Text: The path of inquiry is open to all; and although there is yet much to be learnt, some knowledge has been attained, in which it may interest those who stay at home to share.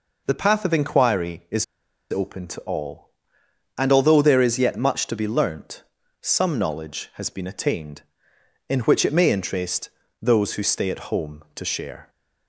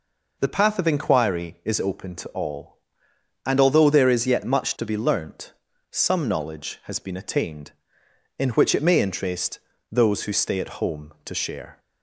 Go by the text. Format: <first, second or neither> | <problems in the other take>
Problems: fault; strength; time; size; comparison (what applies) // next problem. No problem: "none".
second | pauses between "is" and "open"; noticeable; at 1.6 s; 0.46 s long // pauses between "interest" and "those"; slight; at 9.8 s; 0.32 s long; slight in the second